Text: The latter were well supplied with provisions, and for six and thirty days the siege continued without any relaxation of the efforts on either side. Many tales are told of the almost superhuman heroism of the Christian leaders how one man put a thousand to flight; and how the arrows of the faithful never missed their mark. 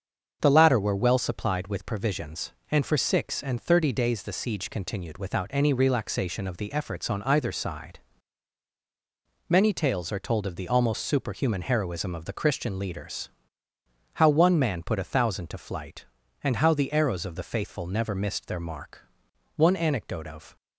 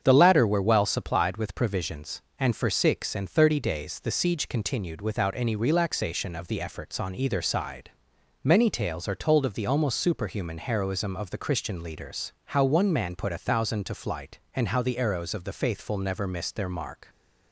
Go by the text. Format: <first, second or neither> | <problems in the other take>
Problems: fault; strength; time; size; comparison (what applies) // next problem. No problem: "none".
second | starts louder than the rest; until 1.4 s; 7 dB; strong in the second // pauses between "leaders" and "how"; noticeable; at 13.2 s; 0.84 s long // goes on to say "One anecdote of"; noticeable; from 19.5 s on; 1.0 s long